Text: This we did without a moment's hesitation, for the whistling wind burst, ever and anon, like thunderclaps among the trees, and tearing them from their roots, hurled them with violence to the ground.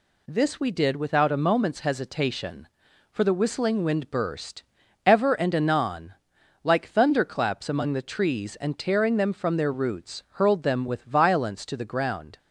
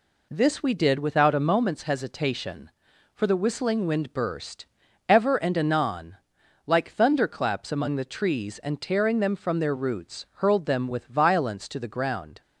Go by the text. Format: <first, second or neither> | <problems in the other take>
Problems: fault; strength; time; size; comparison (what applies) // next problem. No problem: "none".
first | starts louder than the rest; slight; until 1.6 s; 2.5 dB